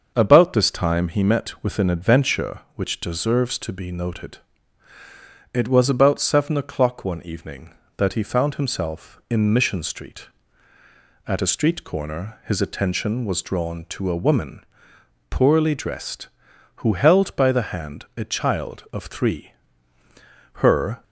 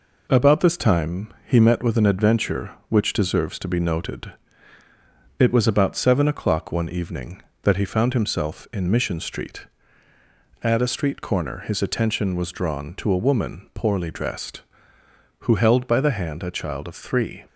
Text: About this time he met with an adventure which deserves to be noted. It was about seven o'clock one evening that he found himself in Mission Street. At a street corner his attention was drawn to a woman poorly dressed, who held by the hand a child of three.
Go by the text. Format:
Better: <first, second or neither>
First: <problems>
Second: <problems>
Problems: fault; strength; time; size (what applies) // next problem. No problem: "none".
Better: second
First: starts louder than the rest; until 1.1 s; 6.5 dB // pauses between "woman" and "poorly"; noticeable; at 14.6 s; 0.68 s long // goes on to say "Her"; slight; from 20.6 s on; 0.42 s long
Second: none